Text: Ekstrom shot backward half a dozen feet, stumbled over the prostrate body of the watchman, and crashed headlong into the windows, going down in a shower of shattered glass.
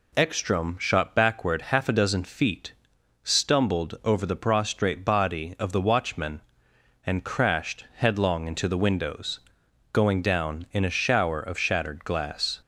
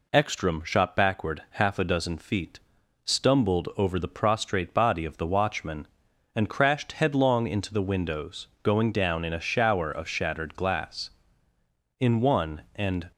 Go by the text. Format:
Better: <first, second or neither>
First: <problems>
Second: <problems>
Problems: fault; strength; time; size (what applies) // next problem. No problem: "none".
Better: first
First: none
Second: goes on to say "In one and"; noticeable; from 11.9 s on; 1.1 s long